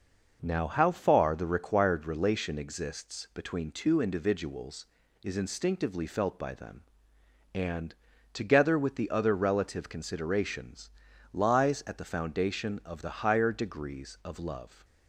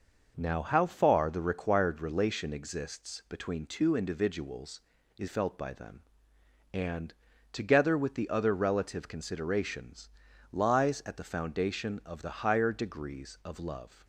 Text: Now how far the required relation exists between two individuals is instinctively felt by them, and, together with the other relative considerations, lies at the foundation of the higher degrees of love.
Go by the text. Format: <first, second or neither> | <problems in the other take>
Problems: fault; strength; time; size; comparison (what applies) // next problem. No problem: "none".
first | skips "instinctively"; at 5.2 s